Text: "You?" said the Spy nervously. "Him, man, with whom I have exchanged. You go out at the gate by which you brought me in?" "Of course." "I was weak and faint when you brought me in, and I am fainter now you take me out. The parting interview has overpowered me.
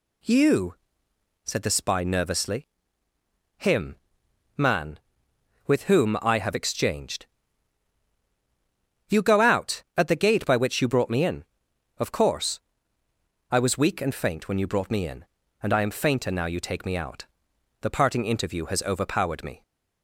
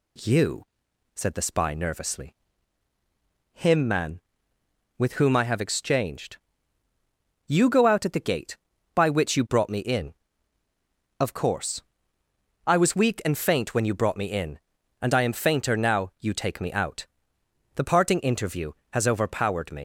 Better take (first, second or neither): first